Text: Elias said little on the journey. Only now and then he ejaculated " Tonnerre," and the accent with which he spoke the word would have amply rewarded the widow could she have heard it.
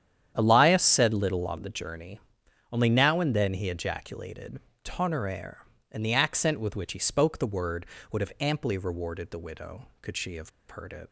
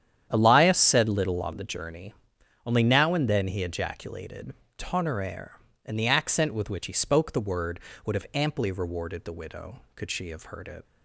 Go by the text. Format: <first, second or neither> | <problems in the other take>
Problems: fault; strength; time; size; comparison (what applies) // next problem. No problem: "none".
second | starts louder than the rest; strong; until 1.3 s; 9.5 dB; strong in the second // pauses between "have" and "heard"; slight; at 10.4 s; 0.19 s long